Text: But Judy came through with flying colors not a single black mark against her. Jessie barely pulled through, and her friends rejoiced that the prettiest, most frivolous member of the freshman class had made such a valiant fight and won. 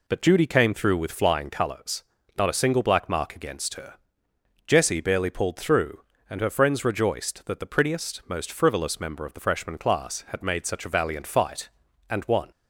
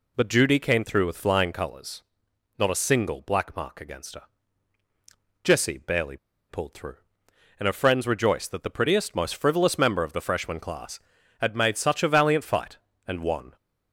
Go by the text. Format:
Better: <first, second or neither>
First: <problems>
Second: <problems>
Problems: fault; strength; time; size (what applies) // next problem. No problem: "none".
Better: first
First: pauses between "colors" and "not"; slight; at 2.0 s; 0.34 s long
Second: pauses between "colors" and "not"; noticeable; at 2.0 s; 0.56 s long // pauses between "barely" and "pulled"; slight; at 6.1 s; 0.33 s long